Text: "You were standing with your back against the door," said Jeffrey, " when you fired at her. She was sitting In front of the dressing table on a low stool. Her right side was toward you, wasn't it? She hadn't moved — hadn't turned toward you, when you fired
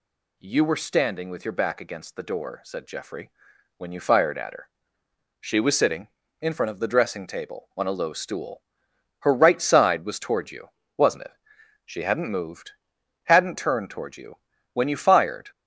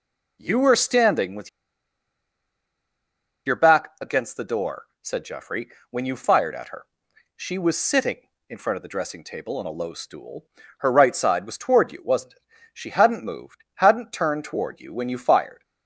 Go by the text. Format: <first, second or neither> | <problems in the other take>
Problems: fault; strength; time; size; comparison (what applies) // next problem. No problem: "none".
first | pauses between "with" and "your"; strong; at 1.4 s; 1.9 s long